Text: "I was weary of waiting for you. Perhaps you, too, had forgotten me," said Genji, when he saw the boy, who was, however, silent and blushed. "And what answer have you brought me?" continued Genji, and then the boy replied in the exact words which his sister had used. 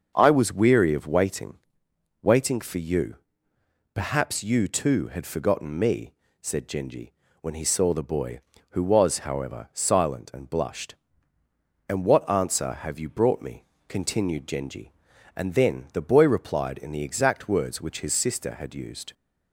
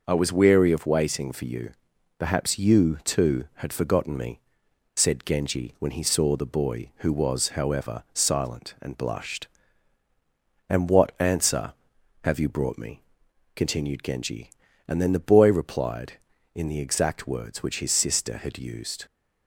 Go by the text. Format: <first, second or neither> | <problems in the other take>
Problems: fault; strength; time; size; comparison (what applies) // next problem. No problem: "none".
second | starts louder than the rest; until 1.1 s; 6 dB // says "waiting" twice; at 2.2 s